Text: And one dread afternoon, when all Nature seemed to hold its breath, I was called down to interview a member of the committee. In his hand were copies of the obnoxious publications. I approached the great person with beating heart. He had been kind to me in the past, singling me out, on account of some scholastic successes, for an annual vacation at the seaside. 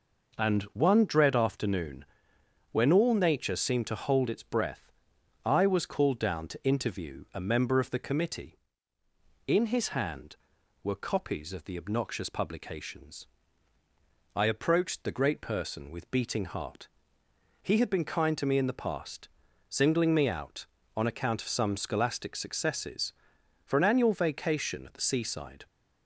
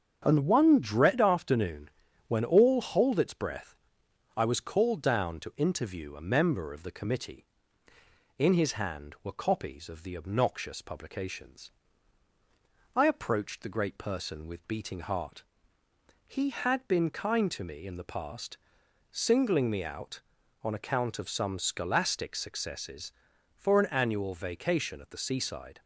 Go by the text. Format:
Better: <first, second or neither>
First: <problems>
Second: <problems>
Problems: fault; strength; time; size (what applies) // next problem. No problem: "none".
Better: first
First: none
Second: starts louder than the rest; strong; until 1.2 s; 7.5 dB // skips "Nature seemed to"; at 2.7 s